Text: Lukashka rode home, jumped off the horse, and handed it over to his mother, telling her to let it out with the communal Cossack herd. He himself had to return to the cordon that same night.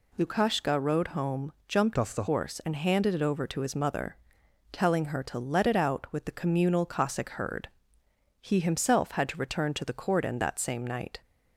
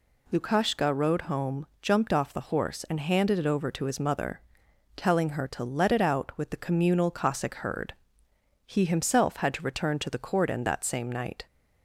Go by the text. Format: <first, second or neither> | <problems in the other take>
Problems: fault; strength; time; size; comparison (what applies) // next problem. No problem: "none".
second | changes voice from "off" to "the"; from 1.9 to 2.2 s; 0.3 s long